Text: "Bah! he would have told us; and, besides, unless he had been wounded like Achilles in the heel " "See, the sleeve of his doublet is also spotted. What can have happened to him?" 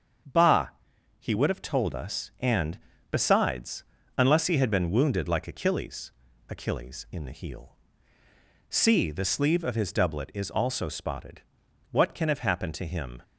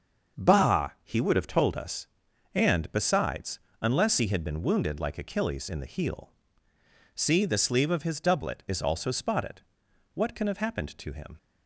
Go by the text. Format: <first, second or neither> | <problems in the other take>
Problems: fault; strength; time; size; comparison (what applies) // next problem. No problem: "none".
second | starts louder than the rest; strong; until 1.7 s; 7.5 dB; also in the second // says "Achilles" twice; at 6.4 s